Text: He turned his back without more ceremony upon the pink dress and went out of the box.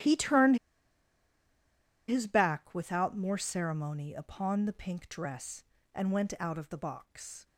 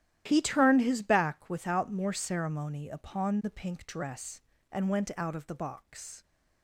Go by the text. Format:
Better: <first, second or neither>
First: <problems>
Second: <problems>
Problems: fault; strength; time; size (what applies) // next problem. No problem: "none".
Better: second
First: starts louder than the rest; strong; until 2.5 s; 12.5 dB // pauses between "turned" and "his"; strong; at 0.5 s; 1.5 s long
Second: starts louder than the rest; strong; until 1.2 s; 12 dB